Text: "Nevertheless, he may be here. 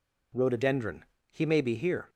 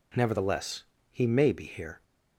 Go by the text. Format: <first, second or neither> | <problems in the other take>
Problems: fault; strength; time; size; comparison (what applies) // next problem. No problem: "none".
second | says "Rhododendron" for "Nevertheless"; at 0.3 s